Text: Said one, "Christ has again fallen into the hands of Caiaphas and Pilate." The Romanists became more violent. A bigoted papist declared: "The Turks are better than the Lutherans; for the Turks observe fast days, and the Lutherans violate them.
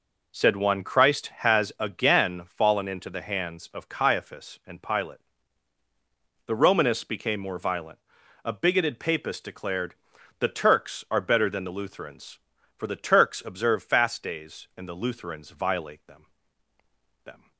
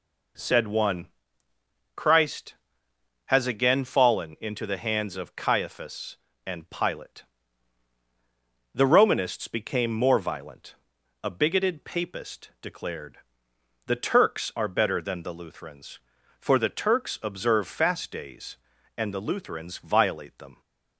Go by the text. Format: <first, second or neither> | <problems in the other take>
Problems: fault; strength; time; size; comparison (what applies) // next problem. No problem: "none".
second | says "them" twice; at 17.2 s